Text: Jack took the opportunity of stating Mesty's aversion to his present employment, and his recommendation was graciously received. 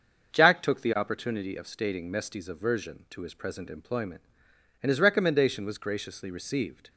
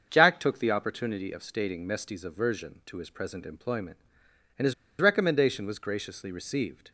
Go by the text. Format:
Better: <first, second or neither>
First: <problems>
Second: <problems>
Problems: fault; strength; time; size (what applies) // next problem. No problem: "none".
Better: first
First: starts louder than the rest; until 1.3 s; 6.5 dB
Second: starts louder than the rest; until 1.1 s; 6.5 dB // pauses between "his" and "recommendation"; slight; at 4.7 s; 0.26 s long